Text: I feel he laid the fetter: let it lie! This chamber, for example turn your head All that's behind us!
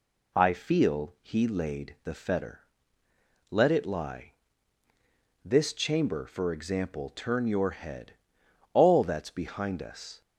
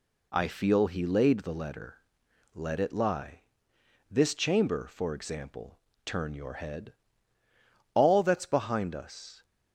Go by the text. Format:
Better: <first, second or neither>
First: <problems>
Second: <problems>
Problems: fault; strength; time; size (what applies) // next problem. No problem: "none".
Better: first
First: pauses between "head" and "All"; noticeable; at 8.1 s; 0.58 s long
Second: says "letter" for "fetter"; at 1.5 s // pauses between "example" and "turn"; slight; at 5.7 s; 0.26 s long // pauses between "head" and "All"; at 6.9 s; 1.0 s long